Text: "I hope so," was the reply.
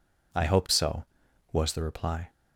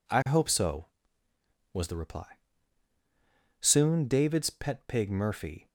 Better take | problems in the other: first | goes on to say "Soon David's pet pig Murphy"; strong; from 3.5 s on; 2.0 s long

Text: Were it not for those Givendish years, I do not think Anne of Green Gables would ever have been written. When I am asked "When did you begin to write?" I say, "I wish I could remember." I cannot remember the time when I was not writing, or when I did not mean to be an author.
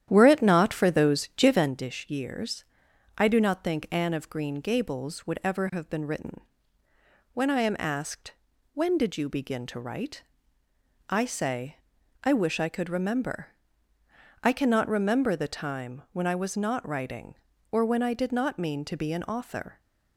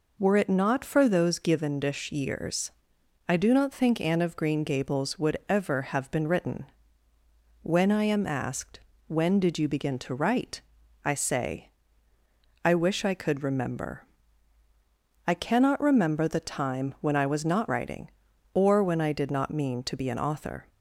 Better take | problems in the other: second | starts louder than the rest; strong; until 1.8 s; 10.5 dB // pauses between "asked" and "When"; at 8.3 s; 0.40 s long; slight in the second

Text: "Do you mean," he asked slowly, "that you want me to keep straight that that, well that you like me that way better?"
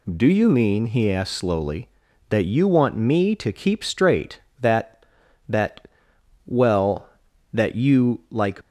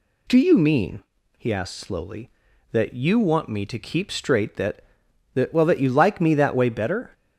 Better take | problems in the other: second | stops before "me that way better"; at 8.6 s

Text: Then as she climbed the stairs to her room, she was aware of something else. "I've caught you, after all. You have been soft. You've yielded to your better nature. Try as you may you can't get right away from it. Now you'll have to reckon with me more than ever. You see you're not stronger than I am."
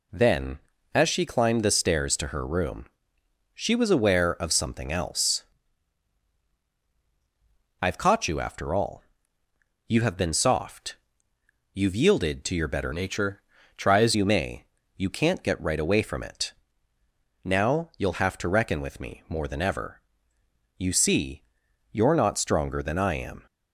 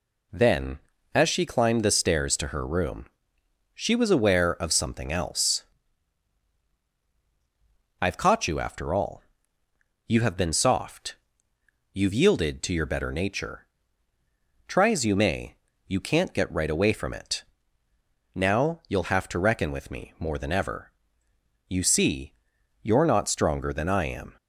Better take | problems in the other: second | changes voice from "nature" to "as"; from 12.9 to 14.1 s; 1.2 s long // pauses between "may" and "you"; slight; at 14.6 s; 0.32 s long; slight in the second // pauses between "see" and "you're"; noticeable; at 21.4 s; 0.48 s long; noticeable in the second

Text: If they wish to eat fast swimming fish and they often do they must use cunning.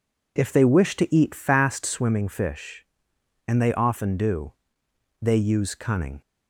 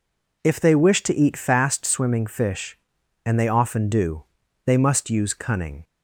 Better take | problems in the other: second | pauses between "do" and "they"; noticeable; at 4.5 s; 0.66 s long; also in the second // skips "must"; at 5.3 s

